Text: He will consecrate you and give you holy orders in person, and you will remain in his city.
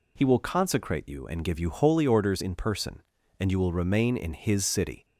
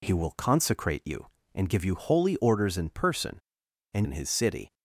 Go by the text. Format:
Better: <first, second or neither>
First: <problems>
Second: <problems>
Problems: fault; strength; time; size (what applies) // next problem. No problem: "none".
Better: first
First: none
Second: skips "you will remain"; at 4.0 s